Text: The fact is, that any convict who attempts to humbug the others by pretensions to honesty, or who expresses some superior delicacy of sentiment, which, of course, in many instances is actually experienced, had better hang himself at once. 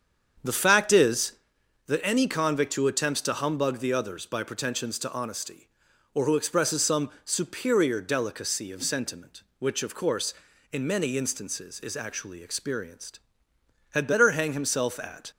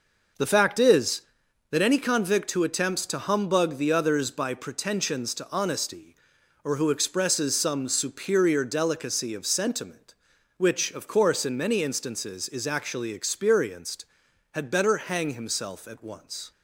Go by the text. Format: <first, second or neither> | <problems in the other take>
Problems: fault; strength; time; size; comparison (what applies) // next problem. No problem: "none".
second | starts louder than the rest; strong; until 1.9 s; 7.5 dB // pauses between "some" and "superior"; slight; at 7.0 s; 0.16 s long // stops before "once"; at 15.3 s